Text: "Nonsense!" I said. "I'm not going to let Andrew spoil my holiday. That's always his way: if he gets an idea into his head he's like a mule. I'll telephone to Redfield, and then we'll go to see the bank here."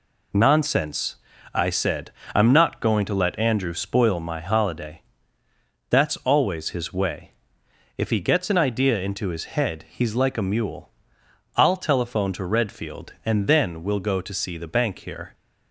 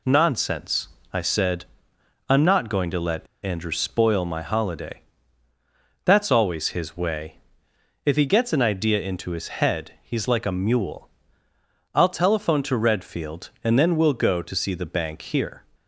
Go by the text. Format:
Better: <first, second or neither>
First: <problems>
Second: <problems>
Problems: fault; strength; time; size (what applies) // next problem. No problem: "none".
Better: first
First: none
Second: pauses between "let" and "Andrew"; slight; at 3.2 s; 0.18 s long